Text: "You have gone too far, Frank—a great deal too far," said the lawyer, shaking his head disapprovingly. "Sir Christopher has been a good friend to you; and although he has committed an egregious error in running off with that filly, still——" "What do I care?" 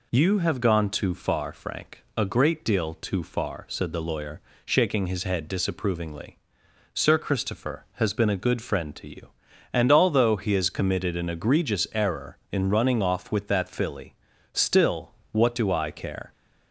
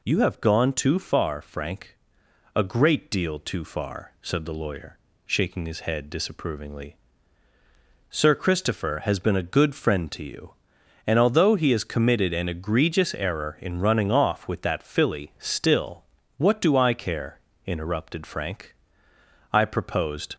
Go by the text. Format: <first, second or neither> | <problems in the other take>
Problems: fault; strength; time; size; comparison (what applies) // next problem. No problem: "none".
first | goes on to say "interrupted Frank I proposed"; strong; from 17.6 s on; 2.7 s long